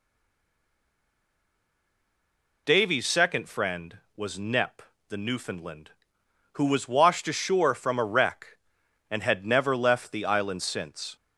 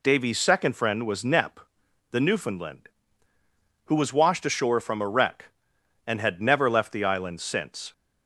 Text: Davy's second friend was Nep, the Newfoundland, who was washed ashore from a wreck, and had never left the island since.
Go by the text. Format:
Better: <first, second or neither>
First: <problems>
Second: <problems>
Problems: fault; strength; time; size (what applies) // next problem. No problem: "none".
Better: second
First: stays silent before the first word; strong; until 2.6 s; 2.6 s long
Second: none